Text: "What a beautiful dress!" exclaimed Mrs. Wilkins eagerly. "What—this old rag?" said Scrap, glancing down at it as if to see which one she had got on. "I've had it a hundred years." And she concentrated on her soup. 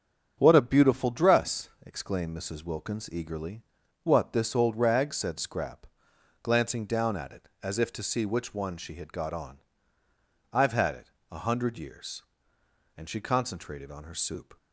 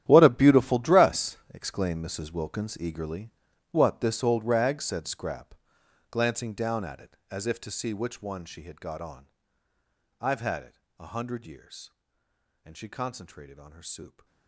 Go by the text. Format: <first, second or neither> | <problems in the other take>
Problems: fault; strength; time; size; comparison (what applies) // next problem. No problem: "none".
first | gets quieter; strong; throughout; 17.5 dB // starts louder than the rest; strong; until 1.0 s; 11 dB; strong in the first // pauses between "it" and "a"; slight; at 10.7 s; 0.18 s long; slight in the first